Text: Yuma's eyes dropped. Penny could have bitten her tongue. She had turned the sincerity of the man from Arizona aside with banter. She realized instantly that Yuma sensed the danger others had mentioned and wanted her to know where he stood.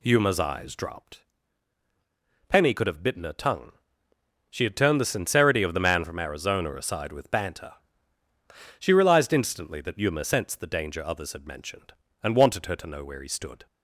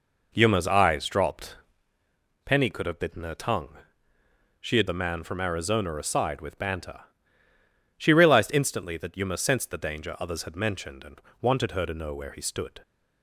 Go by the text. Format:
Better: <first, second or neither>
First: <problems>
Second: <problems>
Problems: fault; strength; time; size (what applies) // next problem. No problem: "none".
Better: first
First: none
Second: skips "turned the sincerity of"; at 4.8 s // pauses between "and" and "wanted"; slight; at 11.2 s; 0.18 s long